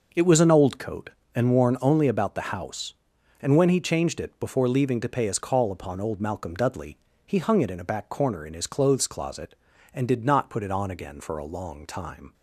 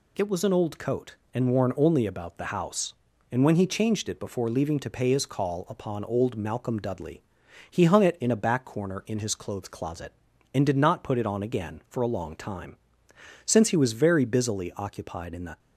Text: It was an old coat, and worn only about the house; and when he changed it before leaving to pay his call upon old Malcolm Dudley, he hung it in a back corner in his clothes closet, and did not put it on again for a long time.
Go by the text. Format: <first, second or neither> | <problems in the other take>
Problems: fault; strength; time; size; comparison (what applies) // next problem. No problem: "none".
first | goes on to say "Since he was very busily occupied in the"; strong; from 13.4 s on; 2.1 s long